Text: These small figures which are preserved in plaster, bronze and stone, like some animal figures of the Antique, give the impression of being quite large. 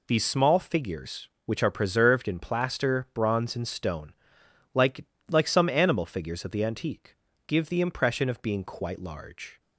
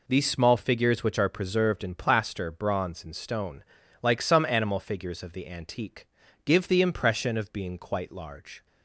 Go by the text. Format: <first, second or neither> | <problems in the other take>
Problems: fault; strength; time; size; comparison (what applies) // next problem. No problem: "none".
second | says "like" twice; at 5.2 s